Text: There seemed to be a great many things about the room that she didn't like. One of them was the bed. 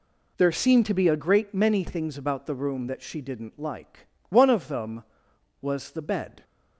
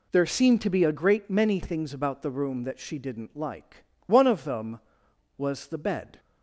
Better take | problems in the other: neither | none

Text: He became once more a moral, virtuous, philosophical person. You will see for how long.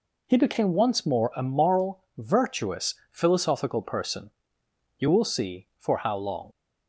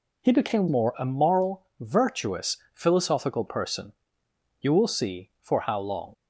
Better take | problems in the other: first | skips "once"; at 0.6 s

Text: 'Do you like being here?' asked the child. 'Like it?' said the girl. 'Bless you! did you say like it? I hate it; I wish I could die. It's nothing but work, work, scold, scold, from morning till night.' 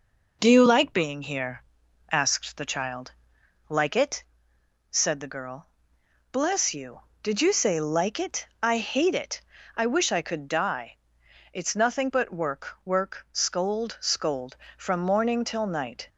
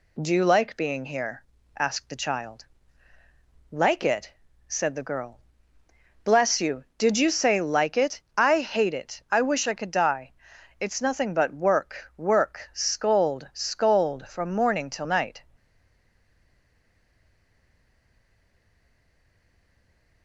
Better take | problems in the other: first | stays silent after the last word; strong; from 15.5 s on; 4.7 s long

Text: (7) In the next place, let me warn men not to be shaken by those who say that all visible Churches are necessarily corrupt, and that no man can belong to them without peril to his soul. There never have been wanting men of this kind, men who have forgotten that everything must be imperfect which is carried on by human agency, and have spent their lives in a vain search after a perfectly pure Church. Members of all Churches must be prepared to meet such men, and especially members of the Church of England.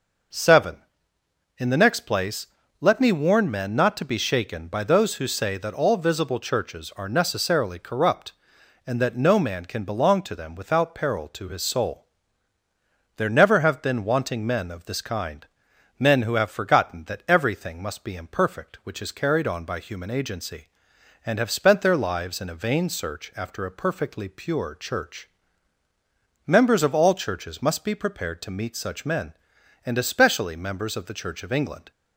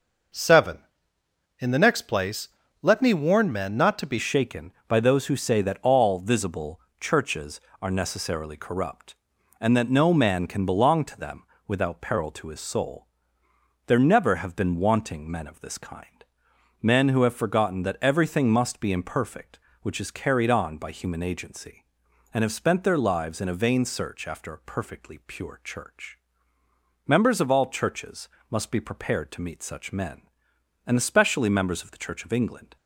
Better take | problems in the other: first | changes voice at "shaken"; from 4.1 s on; 28.6 s long // pauses between "visible" and "Churches"; slight; at 6.7 s; 0.20 s long // pauses between "them" and "without"; slight; at 11.4 s; 0.24 s long // pauses between "Churches" and "must"; slight; at 28.2 s; 0.20 s long

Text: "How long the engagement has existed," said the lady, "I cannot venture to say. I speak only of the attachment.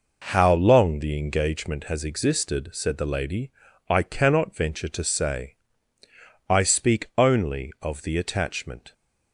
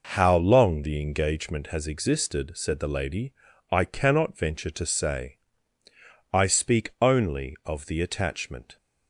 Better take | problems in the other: neither | none

